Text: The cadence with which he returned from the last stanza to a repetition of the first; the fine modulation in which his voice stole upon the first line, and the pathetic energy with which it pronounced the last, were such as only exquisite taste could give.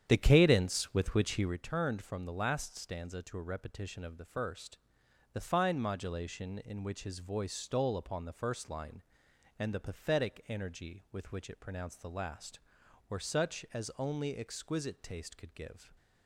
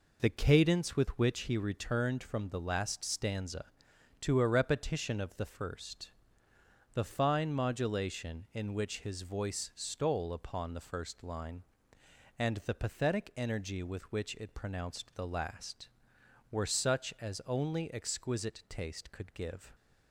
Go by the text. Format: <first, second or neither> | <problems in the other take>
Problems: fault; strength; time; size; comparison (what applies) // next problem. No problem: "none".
second | starts louder than the rest; strong; until 1.6 s; 9.5 dB